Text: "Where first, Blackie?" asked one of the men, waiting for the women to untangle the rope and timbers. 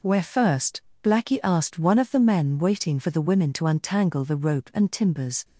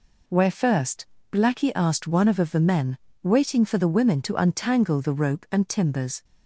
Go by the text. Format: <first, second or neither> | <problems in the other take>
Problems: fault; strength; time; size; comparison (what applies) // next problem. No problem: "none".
first | says "of" twice; at 2.3 s